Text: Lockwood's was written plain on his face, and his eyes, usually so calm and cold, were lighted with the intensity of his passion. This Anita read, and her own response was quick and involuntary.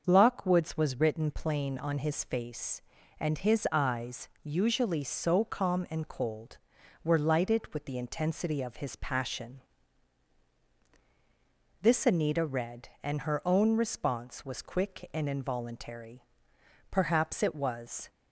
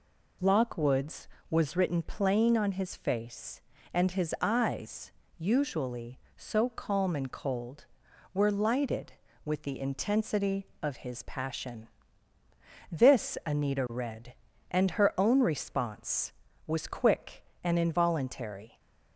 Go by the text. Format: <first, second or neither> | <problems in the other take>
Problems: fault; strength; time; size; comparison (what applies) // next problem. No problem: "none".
second | starts louder than the rest; until 1.0 s; 6.5 dB // goes on to say "Perhaps it was"; noticeable; from 16.9 s on; 1.2 s long